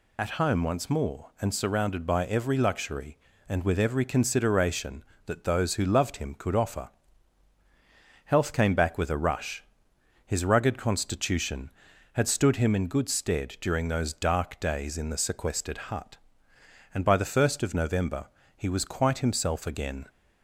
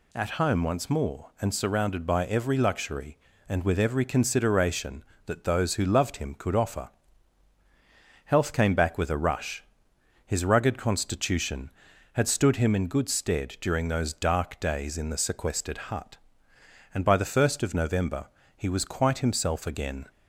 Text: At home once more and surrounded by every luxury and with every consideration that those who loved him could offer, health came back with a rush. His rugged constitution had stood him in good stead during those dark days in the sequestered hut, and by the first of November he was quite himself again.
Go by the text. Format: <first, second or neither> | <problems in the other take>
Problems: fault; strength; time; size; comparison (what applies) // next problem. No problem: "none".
second | loses the start of "At"; at 0.1 s; 55 ms // pauses between "November" and "he"; slight; at 18.2 s; 0.32 s long; slight in the second